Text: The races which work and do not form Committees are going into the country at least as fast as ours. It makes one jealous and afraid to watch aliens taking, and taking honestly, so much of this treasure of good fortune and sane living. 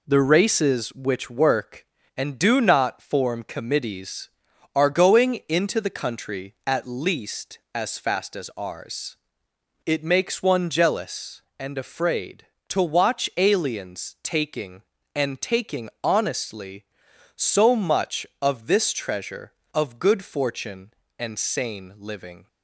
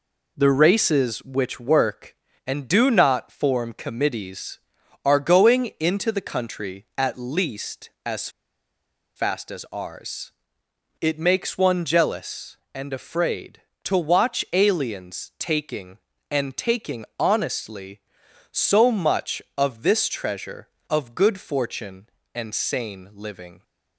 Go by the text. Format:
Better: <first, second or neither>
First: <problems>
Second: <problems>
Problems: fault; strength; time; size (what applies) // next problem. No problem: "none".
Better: first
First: none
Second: pauses between "as" and "fast"; noticeable; at 8.2 s; 0.87 s long